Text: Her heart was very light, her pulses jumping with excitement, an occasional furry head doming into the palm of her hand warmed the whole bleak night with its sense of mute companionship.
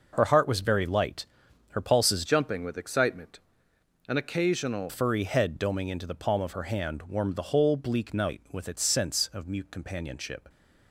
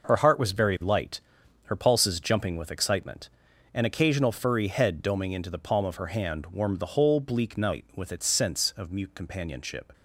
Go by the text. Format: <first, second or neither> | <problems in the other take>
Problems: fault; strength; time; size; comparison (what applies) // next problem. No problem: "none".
second | changes voice from "jumping" to "occasional"; from 2.2 to 4.9 s; 2.7 s long